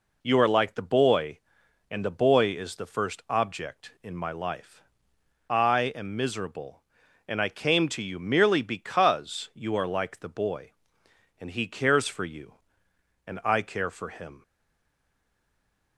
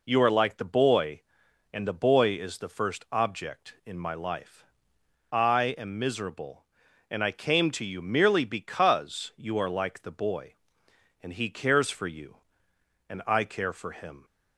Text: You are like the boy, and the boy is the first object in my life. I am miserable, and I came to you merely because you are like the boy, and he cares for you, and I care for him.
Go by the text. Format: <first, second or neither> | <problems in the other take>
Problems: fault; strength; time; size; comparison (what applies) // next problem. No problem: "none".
second | stays silent after the last word; noticeable; from 14.4 s on; 1.5 s long